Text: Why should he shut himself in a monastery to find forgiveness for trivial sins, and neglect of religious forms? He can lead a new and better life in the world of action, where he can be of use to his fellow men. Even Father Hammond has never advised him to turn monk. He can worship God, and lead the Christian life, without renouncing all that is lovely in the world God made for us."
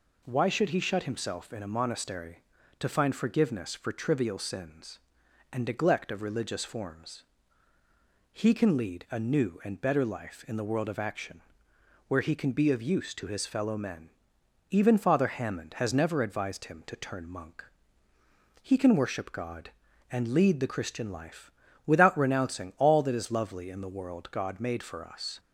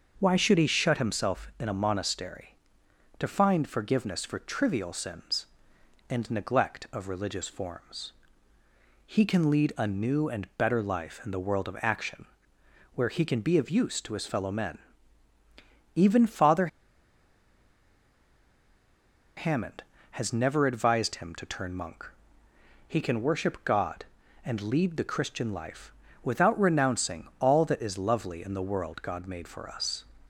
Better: first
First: none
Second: starts louder than the rest; until 1.1 s; 6.5 dB // pauses between "Father" and "Hammond"; strong; at 16.6 s; 2.6 s long

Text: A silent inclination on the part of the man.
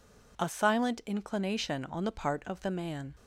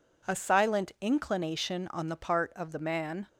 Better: neither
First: none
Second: none

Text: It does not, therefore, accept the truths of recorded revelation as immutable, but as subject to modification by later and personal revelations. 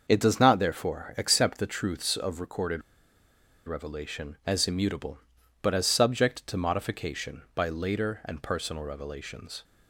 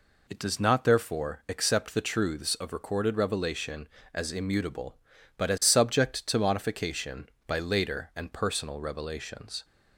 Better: second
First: starts louder than the rest; until 1.0 s; 6.5 dB // pauses between "recorded" and "revelation"; noticeable; at 2.8 s; 0.85 s long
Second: none

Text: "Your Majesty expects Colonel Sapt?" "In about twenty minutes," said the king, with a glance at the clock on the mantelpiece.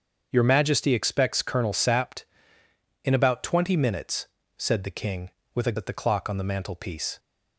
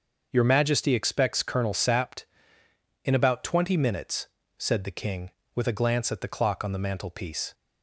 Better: second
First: starts louder than the rest; until 1.3 s; 7 dB // skips "glance"; at 5.7 s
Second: starts louder than the rest; until 1.3 s; 6 dB

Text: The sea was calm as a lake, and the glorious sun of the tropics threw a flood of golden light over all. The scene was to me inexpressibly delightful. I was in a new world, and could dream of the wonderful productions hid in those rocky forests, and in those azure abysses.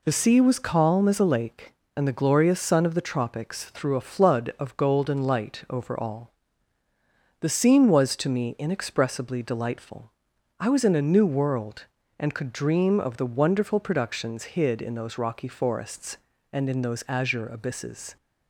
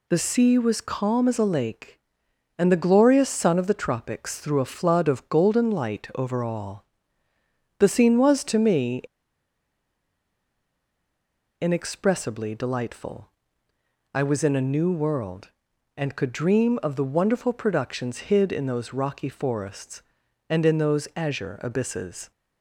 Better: first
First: none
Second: pauses between "me" and "inexpressibly"; strong; at 9.0 s; 2.5 s long

